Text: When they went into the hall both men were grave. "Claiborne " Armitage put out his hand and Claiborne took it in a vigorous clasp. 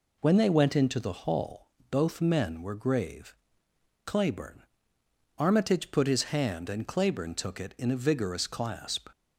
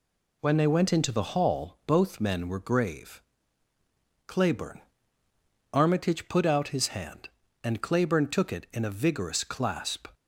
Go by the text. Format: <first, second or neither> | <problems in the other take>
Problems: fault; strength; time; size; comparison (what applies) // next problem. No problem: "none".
second | pauses between "hall" and "both"; slight; at 1.6 s; 0.24 s long // skips "out"; at 6.0 s